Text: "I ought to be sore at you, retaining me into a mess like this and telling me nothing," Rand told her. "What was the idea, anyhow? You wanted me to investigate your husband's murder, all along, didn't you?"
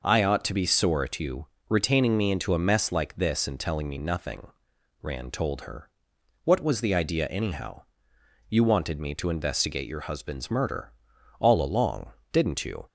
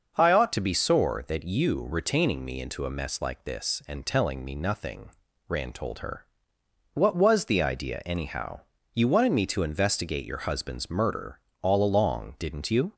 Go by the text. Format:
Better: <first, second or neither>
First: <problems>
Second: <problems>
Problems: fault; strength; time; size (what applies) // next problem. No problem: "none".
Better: first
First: none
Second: starts louder than the rest; noticeable; until 1.2 s; 6 dB // says "that" for "at"; at 1.2 s